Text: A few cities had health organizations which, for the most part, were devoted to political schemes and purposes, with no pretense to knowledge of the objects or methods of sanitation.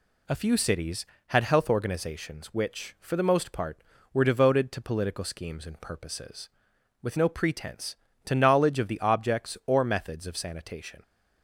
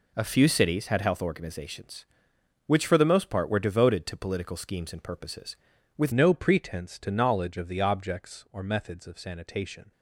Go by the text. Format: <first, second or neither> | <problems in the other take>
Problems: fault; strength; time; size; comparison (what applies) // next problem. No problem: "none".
first | changes voice at "no"; from 6.1 s on; 3.8 s long